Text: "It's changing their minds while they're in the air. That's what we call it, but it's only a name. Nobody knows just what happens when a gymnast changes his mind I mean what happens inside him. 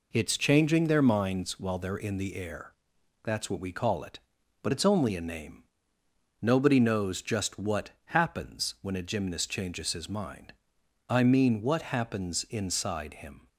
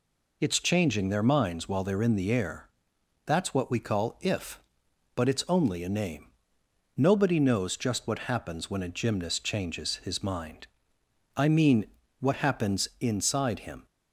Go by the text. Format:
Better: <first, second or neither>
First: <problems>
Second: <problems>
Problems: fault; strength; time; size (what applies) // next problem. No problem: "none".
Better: first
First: pauses between "mind" and "I"; noticeable; at 10.5 s; 0.56 s long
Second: says "if" for "it"; at 4.2 s // pauses between "mind" and "I"; noticeable; at 10.6 s; 0.68 s long // pauses between "mean" and "what"; slight; at 11.8 s; 0.36 s long